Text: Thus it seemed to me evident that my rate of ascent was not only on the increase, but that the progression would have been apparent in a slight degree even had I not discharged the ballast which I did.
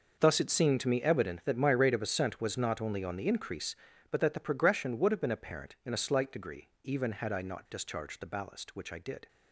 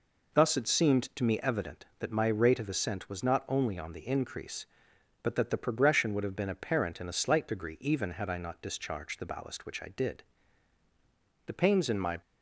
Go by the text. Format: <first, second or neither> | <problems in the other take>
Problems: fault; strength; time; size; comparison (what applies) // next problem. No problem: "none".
first | goes on to say "The pains in my"; noticeable; from 11.4 s on; 0.74 s long